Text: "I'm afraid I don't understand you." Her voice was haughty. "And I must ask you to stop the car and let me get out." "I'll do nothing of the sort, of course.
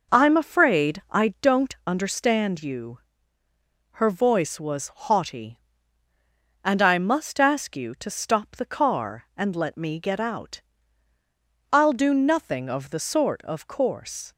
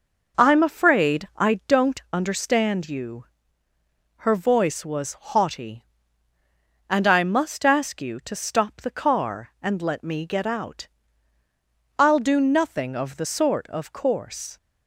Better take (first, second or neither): neither